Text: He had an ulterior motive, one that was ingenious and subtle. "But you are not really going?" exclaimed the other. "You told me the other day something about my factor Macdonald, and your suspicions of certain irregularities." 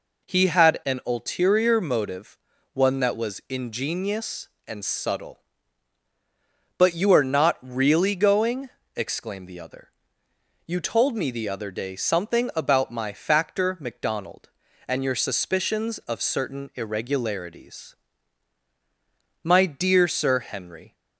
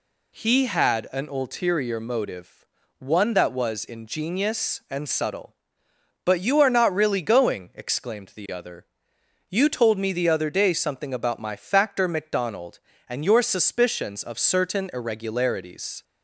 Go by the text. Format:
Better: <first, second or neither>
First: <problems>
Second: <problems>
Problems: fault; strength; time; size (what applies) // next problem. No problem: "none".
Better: second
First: goes on to say "My dear Sir Henry"; from 19.4 s on; 1.5 s long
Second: none